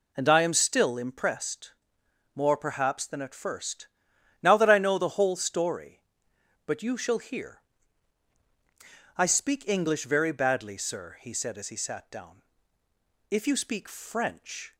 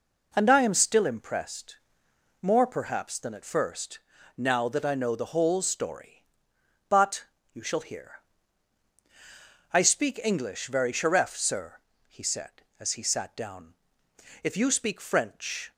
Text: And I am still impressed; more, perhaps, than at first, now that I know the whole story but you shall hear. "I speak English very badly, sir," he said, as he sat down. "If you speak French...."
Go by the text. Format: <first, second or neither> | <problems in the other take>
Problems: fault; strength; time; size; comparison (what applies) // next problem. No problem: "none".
first | pauses between "but" and "you"; slight; at 7.2 s; 0.28 s long // says "sheref" for "badly"; at 10.9 s